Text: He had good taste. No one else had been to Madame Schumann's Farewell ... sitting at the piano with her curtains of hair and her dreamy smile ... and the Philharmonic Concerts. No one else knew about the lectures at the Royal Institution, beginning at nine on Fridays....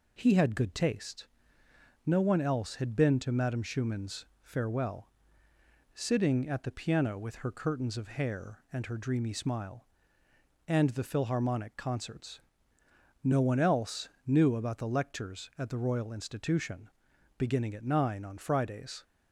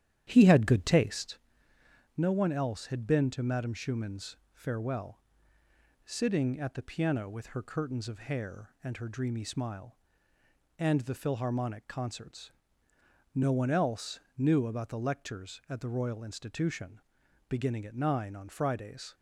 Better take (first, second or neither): first